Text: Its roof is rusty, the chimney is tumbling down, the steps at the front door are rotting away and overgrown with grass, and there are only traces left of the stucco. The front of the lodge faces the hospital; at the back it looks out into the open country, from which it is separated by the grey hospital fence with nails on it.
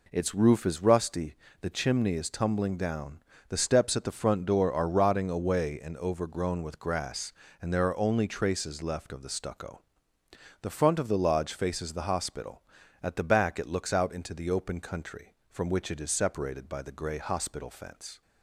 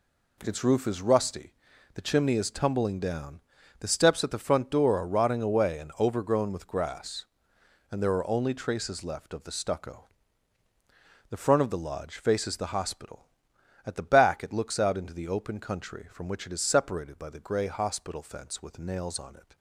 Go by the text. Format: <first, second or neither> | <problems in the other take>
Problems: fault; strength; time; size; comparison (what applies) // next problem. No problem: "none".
second | stops before "with nails on it"; at 18.2 s